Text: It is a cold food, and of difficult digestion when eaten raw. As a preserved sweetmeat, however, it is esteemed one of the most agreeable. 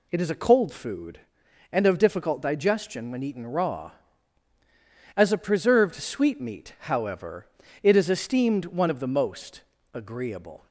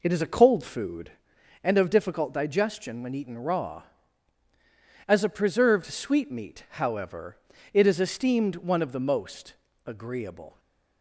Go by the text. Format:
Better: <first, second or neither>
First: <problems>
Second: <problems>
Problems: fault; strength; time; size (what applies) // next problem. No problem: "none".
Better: first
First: pauses between "most" and "agreeable"; slight; at 9.6 s; 0.32 s long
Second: starts louder than the rest; noticeable; until 1.8 s; 4 dB // pauses between "most" and "agreeable"; slight; at 9.5 s; 0.32 s long // stays silent after the last word; slight; from 10.4 s on; 0.6 s long